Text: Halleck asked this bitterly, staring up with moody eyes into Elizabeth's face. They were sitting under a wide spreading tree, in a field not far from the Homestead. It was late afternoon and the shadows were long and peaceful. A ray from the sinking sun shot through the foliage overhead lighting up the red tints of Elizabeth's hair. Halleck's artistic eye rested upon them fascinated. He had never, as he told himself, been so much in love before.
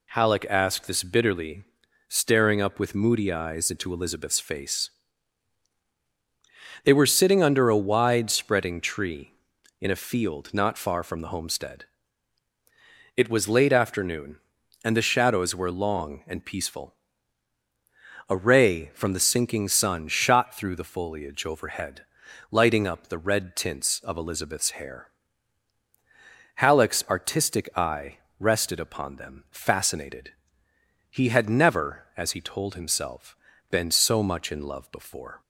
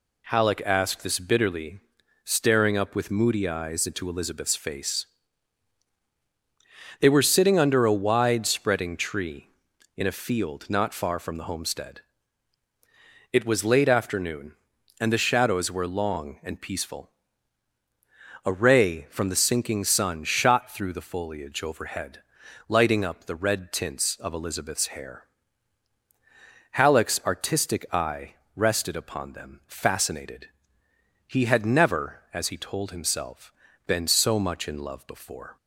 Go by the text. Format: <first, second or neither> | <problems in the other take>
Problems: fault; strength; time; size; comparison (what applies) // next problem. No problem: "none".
neither | pauses between "overhead" and "lighting"; noticeable; the same in both // pauses between "eye" and "rested"; slight; the same in both